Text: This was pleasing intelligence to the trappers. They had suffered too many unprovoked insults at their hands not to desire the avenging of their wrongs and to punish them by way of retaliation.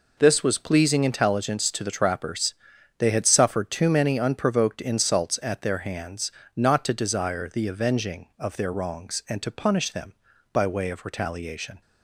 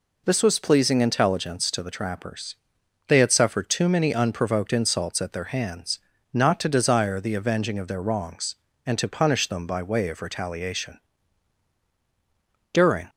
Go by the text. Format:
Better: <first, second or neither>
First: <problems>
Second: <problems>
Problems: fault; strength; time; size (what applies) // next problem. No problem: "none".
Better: first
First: pauses between "hands" and "not"; slight; at 6.3 s; 0.24 s long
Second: pauses between "hands" and "not"; slight; at 5.9 s; 0.34 s long // goes on to say "During"; slight; from 12.7 s on; 0.38 s long